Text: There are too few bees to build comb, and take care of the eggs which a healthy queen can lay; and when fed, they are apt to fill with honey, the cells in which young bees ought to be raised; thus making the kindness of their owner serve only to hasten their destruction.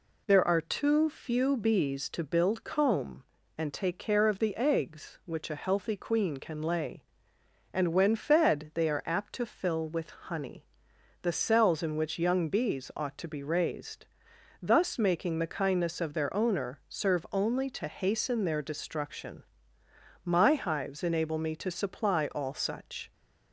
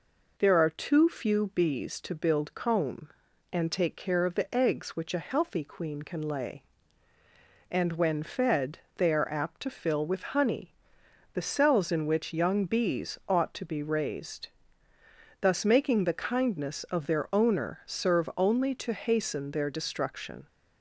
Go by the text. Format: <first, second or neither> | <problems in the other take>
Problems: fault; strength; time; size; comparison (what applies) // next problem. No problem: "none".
second | goes on to say "My hives enable me to supply all such"; strong; from 20.2 s on; 2.8 s long